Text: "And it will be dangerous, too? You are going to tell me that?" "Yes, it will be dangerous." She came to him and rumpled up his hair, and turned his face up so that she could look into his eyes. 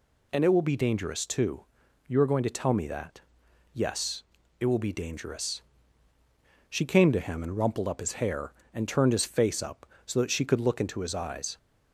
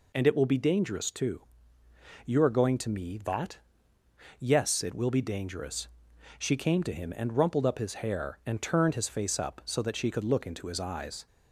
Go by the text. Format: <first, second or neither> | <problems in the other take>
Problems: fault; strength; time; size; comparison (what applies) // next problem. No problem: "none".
first | skips "tell"; at 2.8 s